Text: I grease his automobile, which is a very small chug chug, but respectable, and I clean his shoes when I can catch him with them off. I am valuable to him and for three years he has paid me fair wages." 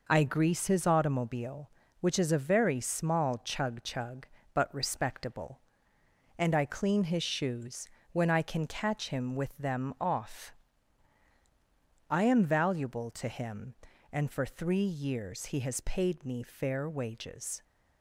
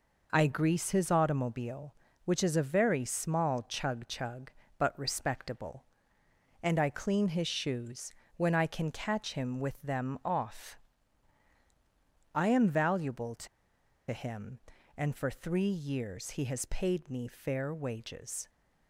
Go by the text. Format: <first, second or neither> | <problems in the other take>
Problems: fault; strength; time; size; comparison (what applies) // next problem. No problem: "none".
first | pauses between "shoes" and "when"; slight; at 8.1 s; 0.24 s long; slight in the first // pauses between "to" and "him"; noticeable; at 13.4 s; 0.63 s long